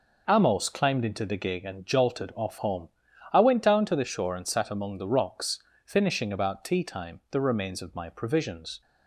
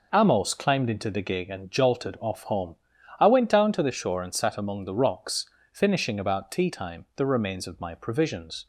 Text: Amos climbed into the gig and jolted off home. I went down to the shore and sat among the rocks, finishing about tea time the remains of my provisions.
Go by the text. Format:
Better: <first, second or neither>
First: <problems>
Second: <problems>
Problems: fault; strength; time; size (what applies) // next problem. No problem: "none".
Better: neither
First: none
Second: none